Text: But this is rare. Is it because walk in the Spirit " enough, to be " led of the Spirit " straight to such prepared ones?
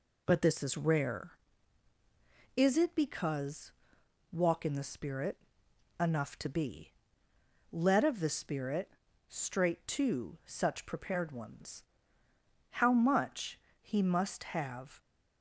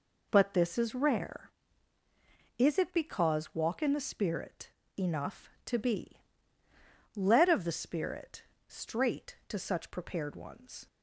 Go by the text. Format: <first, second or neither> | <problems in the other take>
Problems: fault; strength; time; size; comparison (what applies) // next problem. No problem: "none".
second | pauses between "because" and "walk"; noticeable; at 3.7 s; 0.60 s long // goes on to say "How much He must have"; strong; from 12.7 s on; 2.3 s long